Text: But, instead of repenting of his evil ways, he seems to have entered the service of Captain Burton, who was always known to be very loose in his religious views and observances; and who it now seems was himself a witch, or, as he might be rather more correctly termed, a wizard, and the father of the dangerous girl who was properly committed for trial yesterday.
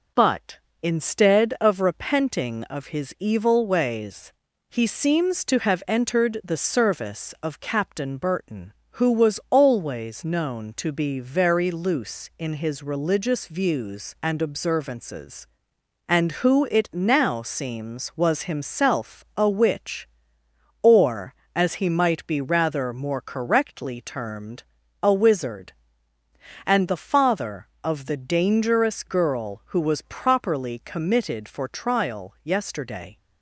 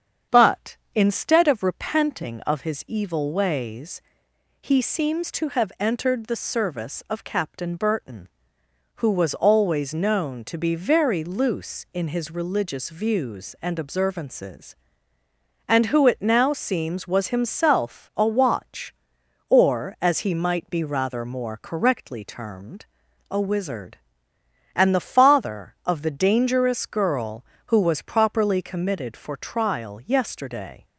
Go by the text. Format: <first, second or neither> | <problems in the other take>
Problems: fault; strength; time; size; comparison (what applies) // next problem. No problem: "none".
first | starts louder than the rest; strong; until 1.4 s; 8 dB // says "watch" for "witch"; at 18.2 s